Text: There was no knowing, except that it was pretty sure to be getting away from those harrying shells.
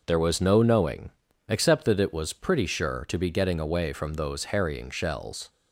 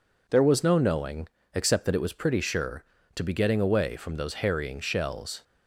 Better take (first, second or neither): second